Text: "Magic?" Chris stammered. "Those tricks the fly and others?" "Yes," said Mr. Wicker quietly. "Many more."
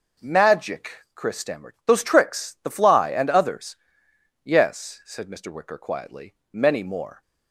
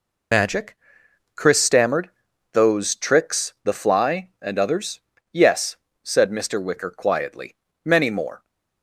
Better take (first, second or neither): first